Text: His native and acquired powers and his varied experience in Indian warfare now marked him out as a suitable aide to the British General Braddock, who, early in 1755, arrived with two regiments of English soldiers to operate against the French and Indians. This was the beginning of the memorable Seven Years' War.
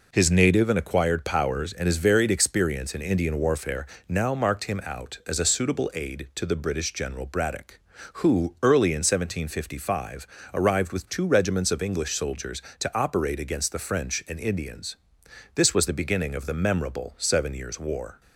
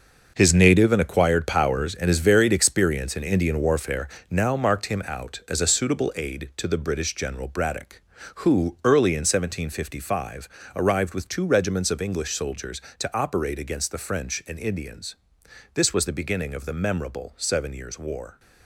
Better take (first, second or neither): first